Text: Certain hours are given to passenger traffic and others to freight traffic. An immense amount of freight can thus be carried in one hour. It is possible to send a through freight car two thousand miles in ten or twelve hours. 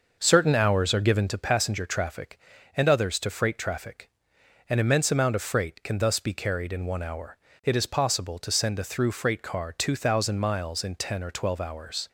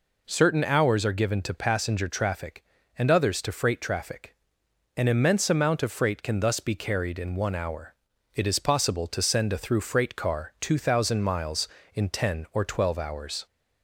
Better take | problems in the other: second | starts louder than the rest; noticeable; until 1.4 s; 6 dB

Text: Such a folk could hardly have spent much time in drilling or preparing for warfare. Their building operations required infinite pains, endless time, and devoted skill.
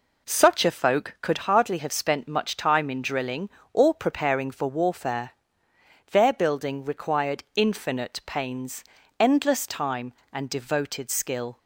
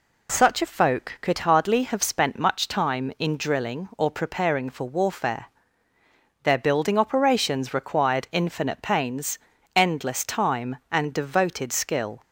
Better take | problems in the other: second | skips "operations"; at 6.8 s

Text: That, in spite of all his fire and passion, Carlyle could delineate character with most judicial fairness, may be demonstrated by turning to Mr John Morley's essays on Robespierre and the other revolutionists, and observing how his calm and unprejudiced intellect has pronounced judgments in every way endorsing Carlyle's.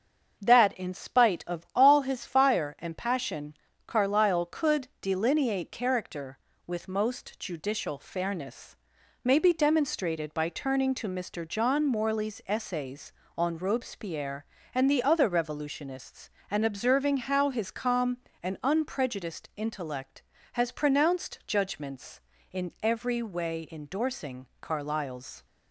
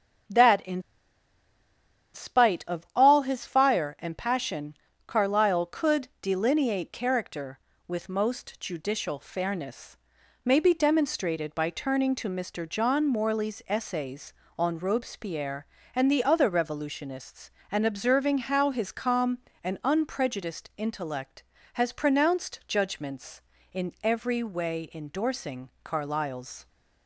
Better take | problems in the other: first | starts louder than the rest; until 2.6 s; 6.5 dB; also in the first // pauses between "in" and "spite"; strong; at 0.8 s; 1.3 s long

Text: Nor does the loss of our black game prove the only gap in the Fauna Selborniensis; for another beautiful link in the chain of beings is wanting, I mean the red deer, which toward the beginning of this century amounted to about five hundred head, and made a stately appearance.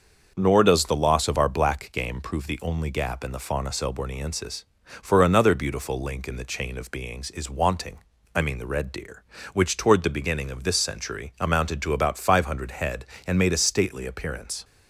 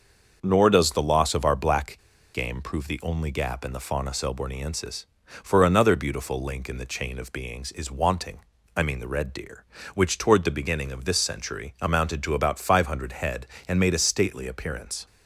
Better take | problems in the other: first | starts louder than the rest; noticeable; until 1.4 s; 6 dB; noticeable in the first // pauses between "black" and "game"; slight; at 1.9 s; 0.35 s long

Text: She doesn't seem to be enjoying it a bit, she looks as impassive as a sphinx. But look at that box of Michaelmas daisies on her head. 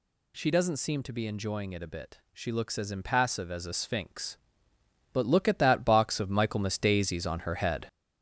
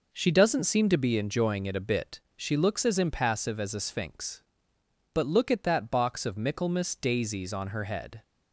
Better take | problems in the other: second | gets louder; noticeable; throughout; 6 dB

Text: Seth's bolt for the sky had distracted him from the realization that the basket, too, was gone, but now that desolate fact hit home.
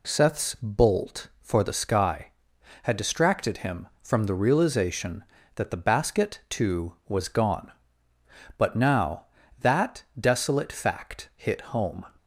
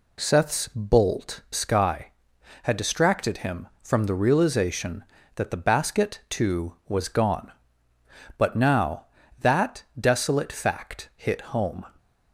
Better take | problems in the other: first | skips "for the"; at 1.4 s // pauses between "that" and "desolate"; slight; at 9.8 s; 0.16 s long; slight in the first

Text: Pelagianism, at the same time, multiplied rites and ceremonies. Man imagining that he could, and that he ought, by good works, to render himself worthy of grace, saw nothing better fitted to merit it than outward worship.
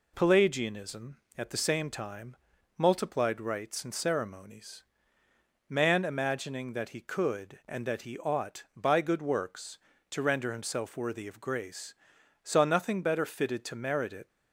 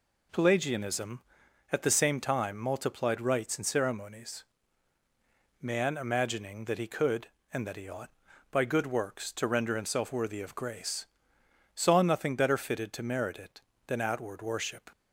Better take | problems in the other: second | stops before "than outward worship"; at 14.2 s

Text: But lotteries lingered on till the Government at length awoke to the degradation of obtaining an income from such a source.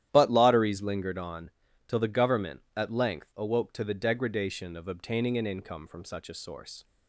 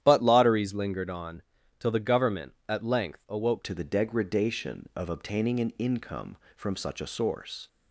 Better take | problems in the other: first | starts louder than the rest; strong; until 1.0 s; 11 dB; strong in the first // pauses between "on" and "till"; slight; at 1.4 s; 0.36 s long; slight in the first // changes voice at "to"; from 3.6 s on; 4.0 s long

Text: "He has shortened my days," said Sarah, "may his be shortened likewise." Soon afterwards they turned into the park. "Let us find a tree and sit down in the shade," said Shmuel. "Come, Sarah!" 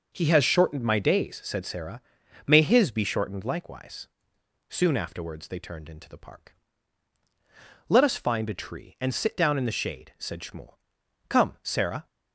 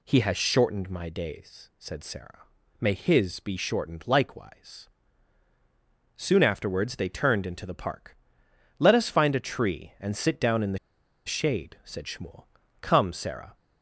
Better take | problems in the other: first | pauses between "the" and "shade"; noticeable; at 10.7 s; 0.48 s long

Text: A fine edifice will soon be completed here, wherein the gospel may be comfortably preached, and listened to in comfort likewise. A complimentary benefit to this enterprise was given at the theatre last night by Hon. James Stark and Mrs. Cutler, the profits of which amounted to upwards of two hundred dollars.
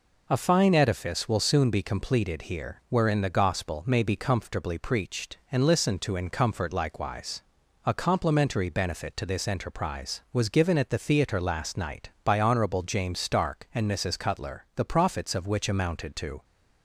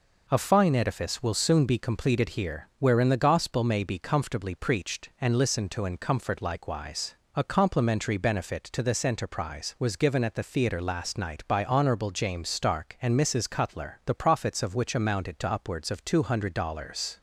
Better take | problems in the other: second | stops before "upwards of two hundred dollars"; at 16.4 s

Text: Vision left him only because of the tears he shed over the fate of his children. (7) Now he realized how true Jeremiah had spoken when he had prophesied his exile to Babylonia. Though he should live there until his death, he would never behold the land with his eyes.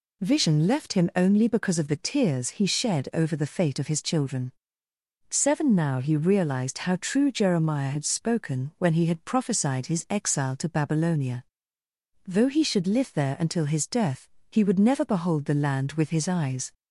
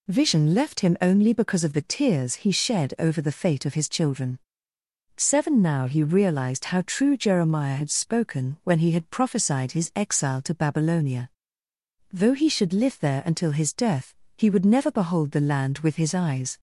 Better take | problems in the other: neither | none

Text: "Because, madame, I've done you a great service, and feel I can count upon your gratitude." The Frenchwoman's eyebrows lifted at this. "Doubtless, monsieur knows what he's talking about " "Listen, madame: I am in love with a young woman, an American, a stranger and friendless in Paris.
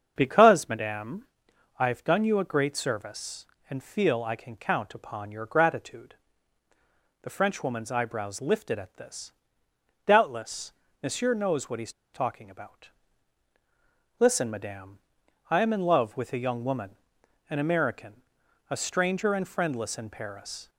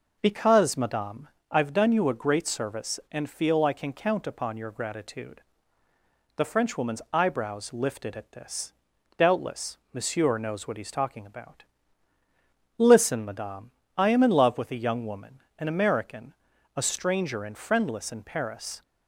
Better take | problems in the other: second | starts louder than the rest; until 1.1 s; 7 dB // pauses between "he's" and "talking"; slight; at 11.9 s; 0.22 s long

